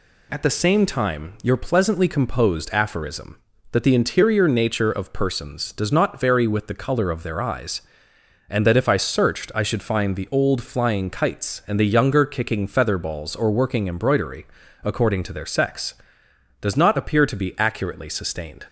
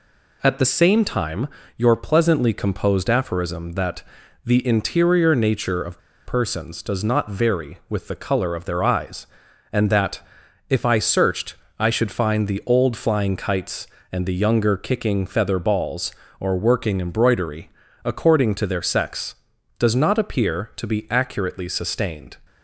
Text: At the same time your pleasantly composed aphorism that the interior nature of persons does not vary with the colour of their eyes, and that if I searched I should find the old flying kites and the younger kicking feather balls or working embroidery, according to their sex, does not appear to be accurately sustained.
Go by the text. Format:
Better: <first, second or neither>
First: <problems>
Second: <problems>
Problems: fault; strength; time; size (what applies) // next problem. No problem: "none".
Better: first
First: none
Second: pauses between "time" and "your"; slight; at 1.4 s; 0.28 s long // pauses between "that" and "the"; at 4.0 s; 0.44 s long // pauses between "of" and "persons"; slight; at 5.9 s; 0.26 s long // pauses between "that" and "if"; noticeable; at 10.1 s; 0.50 s long // pauses between "searched" and "I"; slight; at 11.5 s; 0.24 s long